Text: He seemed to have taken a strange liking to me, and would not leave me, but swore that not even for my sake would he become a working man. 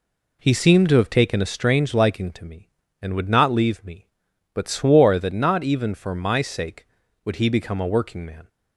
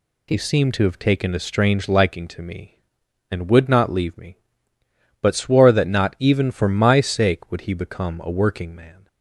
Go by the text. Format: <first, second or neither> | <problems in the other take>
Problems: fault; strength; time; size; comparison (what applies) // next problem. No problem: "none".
neither | none